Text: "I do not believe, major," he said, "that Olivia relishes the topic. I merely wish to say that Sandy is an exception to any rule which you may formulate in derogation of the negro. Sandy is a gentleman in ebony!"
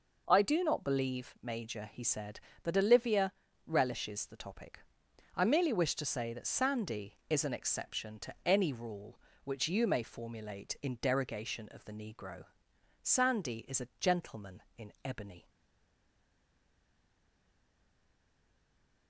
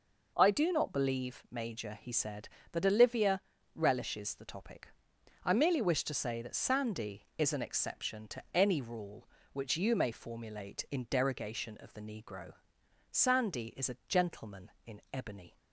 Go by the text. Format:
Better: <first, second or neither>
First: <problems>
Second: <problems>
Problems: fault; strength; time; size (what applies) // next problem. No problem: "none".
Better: second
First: pauses between "Olivia" and "relishes"; slight; at 3.3 s; 0.34 s long // stays silent after the last word; strong; from 15.4 s on; 3.6 s long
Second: pauses between "Olivia" and "relishes"; slight; at 3.4 s; 0.34 s long